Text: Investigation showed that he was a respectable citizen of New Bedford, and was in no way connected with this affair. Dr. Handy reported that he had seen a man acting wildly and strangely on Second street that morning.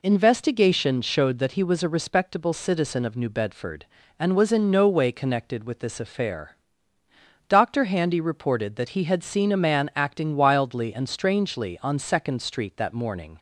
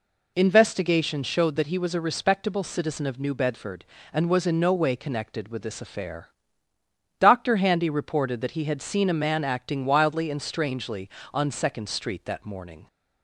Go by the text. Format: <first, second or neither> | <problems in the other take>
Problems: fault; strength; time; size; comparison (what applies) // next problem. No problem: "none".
neither | none